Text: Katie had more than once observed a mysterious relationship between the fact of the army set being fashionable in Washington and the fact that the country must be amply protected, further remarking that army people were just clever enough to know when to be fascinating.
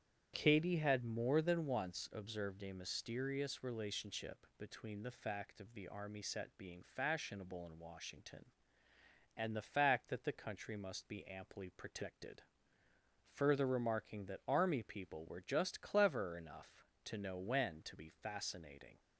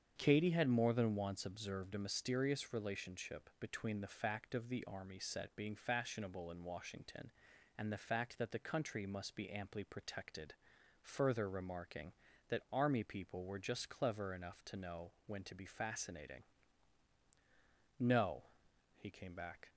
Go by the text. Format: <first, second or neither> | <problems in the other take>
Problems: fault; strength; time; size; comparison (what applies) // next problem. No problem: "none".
first | starts louder than the rest; strong; until 1.1 s; 7.5 dB; strong in the first // pauses between "know" and "when"; slight; at 15.1 s; 0.16 s long // goes on to say "No he came back"; strong; from 17.9 s on; 1.7 s long